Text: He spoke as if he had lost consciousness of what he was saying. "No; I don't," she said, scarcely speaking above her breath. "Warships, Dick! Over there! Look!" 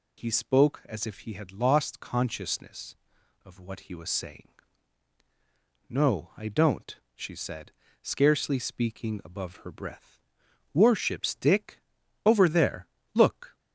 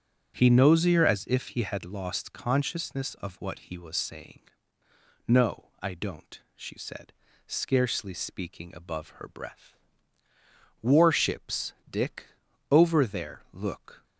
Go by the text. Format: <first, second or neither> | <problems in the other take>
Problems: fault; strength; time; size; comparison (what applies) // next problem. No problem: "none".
first | starts louder than the rest; noticeable; until 1.4 s; 6 dB // says "nosier" for "spoke"; at 0.4 s